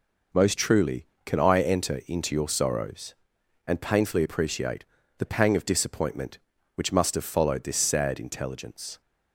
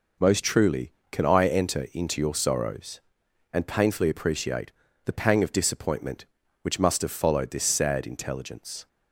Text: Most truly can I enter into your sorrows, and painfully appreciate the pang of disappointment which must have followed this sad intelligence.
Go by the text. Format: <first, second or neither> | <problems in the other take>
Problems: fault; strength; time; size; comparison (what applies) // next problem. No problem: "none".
neither | pauses between "appreciate" and "the"; slight; the same in both